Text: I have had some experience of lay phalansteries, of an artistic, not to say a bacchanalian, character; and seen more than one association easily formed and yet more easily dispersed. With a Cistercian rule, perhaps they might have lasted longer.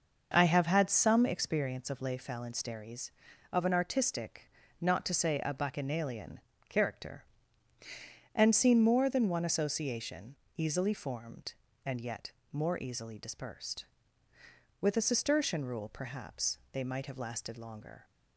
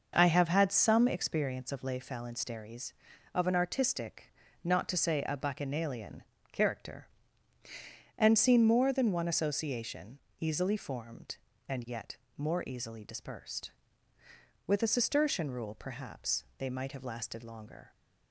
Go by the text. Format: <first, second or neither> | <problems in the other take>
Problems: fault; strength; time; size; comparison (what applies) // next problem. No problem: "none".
neither | starts louder than the rest; noticeable; the same in both // pauses between "association" and "easily"; slight; the same in both // pauses between "yet" and "more"; slight; the same in both